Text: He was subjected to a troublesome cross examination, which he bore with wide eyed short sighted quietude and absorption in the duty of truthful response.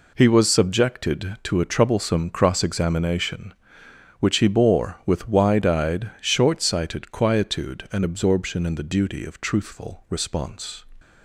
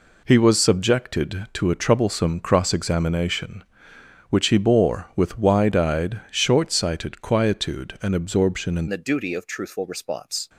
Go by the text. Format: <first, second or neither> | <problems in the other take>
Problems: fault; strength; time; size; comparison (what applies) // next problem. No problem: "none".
first | changes voice at "the"; from 8.8 s on; 1.6 s long